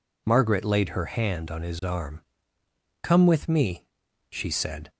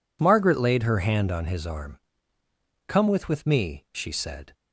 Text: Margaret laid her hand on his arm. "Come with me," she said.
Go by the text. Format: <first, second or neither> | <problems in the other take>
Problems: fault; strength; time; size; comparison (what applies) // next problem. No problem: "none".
first | says "with" twice; at 3.2 s